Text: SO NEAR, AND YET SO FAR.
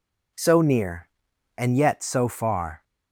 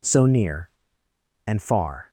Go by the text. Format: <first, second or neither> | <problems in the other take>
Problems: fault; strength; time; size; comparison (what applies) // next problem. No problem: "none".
first | skips "YET SO"; at 1.6 s